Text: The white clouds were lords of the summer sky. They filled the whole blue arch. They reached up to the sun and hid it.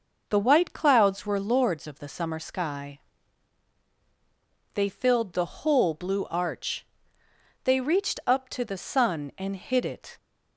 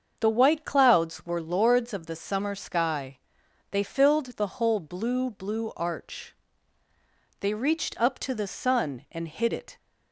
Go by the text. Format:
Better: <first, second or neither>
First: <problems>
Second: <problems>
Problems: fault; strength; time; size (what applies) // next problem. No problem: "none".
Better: first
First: none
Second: starts louder than the rest; until 1.2 s; 7 dB // says "blue" twice; at 5.2 s